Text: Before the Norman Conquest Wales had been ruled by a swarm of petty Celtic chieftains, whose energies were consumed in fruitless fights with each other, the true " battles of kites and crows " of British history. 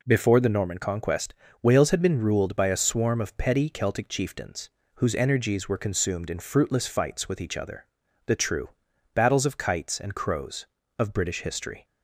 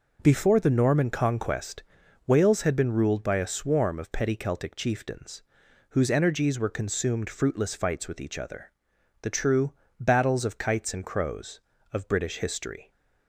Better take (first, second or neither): first